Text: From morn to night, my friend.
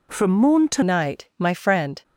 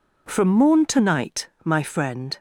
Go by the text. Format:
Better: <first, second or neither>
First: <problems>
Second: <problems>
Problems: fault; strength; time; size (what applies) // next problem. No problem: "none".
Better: second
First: changes voice at "night"; from 0.8 s on; 1.2 s long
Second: none